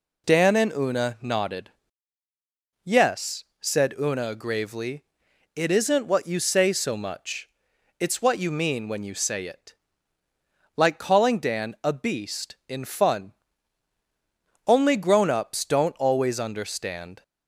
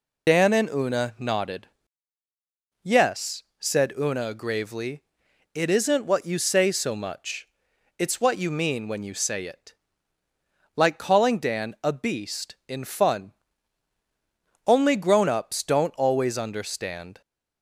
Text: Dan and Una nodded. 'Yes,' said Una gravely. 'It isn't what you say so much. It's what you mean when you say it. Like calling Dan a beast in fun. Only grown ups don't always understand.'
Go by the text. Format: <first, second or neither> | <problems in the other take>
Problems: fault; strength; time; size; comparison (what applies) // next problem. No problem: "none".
first | loses the start of "Dan"; at 0.2 s; 50 ms